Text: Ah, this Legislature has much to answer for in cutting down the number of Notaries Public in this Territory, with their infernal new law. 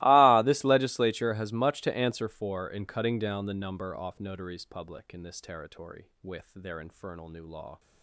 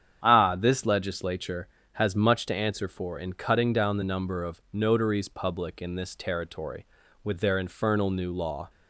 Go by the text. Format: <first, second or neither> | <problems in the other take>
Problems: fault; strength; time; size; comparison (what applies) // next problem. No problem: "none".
second | starts louder than the rest; strong; until 1.0 s; 19.5 dB; strong in the second // says "off" for "of"; at 3.9 s